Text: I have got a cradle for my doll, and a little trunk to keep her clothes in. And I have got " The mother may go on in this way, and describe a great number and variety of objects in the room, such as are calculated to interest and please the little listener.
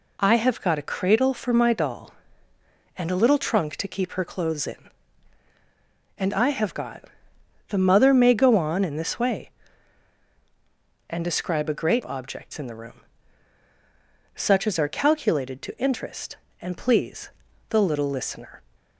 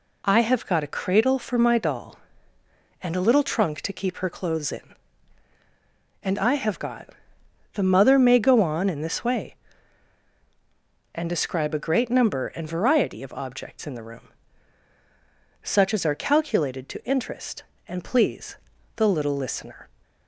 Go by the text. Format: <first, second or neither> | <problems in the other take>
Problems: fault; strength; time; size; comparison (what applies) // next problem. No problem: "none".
second | skips "number and variety of"; at 12.0 s // pauses between "please" and "the"; at 17.3 s; 0.40 s long; also in the second